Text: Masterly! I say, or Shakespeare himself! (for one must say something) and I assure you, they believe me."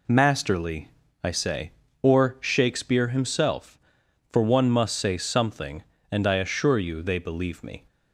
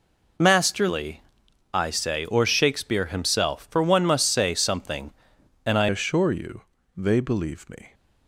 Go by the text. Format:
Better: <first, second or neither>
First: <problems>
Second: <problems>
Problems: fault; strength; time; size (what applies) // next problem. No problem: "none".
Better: first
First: none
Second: changes voice at "assure"; from 5.8 s on; 2.1 s long